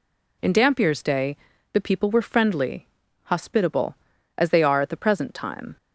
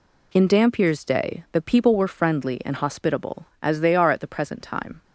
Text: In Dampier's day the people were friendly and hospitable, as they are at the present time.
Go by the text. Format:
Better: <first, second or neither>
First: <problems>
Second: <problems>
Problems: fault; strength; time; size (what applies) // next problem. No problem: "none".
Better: second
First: pauses between "day" and "the"; slight; at 1.3 s; 0.36 s long // skips "and"; at 3.0 s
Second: none